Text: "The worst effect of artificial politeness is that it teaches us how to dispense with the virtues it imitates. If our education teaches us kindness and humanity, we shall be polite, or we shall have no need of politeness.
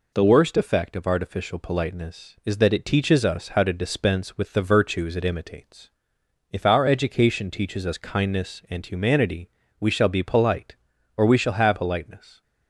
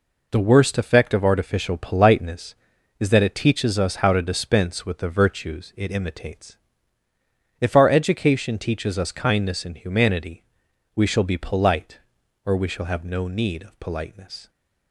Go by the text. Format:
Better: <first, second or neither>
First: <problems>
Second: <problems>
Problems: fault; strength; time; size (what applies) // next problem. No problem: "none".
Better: second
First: skips "no need of"; at 11.7 s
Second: none